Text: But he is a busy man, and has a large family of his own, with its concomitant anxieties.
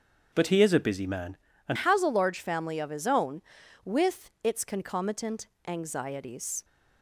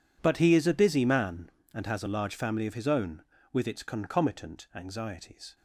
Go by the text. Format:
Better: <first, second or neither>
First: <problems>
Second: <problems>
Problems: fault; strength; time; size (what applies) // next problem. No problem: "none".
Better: second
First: starts louder than the rest; strong; until 1.3 s; 7.5 dB // changes voice at "has"; from 1.7 s on; 4.9 s long // pauses between "concomitant" and "anxieties"; slight; at 5.4 s; 0.20 s long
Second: none